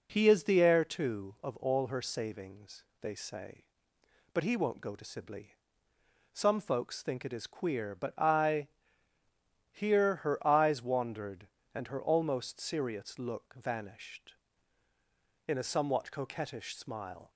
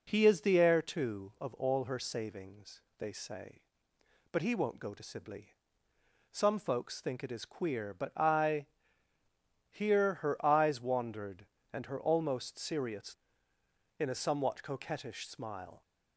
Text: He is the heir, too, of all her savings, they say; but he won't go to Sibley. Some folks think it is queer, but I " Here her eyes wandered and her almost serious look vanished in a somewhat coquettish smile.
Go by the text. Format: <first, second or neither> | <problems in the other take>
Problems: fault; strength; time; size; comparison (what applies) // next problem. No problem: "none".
first | skips "look vanished"; at 13.5 s